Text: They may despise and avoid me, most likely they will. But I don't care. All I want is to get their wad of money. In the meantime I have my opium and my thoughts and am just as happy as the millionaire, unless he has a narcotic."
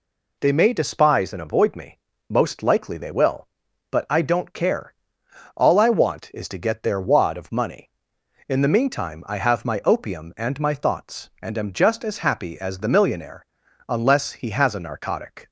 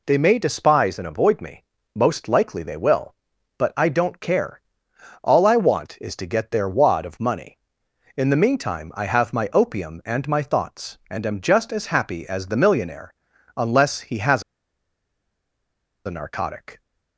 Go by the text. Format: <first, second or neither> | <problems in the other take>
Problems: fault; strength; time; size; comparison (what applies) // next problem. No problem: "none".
first | pauses between "has" and "a"; strong; at 14.4 s; 1.6 s long